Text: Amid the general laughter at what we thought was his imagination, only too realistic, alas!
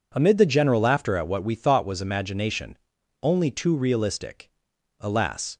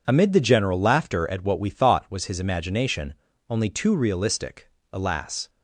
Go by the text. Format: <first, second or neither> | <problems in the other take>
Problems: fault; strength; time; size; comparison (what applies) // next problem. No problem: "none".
second | skips "his"; at 1.9 s